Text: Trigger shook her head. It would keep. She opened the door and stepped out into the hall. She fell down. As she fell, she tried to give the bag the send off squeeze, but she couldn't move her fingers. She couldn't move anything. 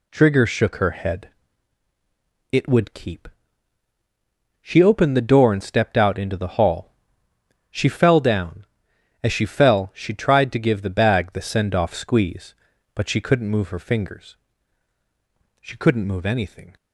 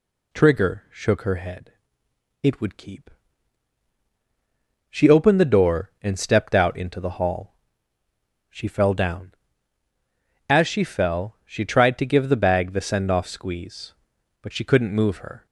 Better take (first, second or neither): first